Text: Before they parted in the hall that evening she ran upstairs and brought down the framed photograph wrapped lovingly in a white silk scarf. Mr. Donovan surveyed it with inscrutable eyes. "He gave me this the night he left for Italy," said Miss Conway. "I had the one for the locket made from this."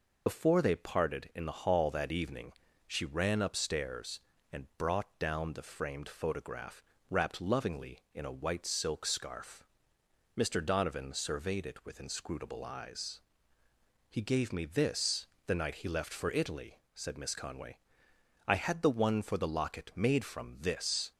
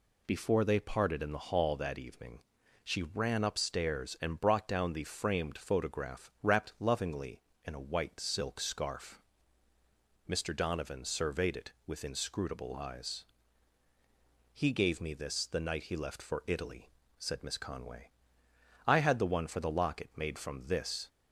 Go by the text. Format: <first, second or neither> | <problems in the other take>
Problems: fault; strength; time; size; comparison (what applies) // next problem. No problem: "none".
second | loses the start of "Before"; at 0.2 s; 45 ms // pauses between "evening" and "she"; slight; at 2.5 s; 0.34 s long; also in the second // pauses between "photograph" and "wrapped"; slight; at 6.8 s; 0.28 s long // pauses between "this" and "the"; slight; at 15.2 s; 0.20 s long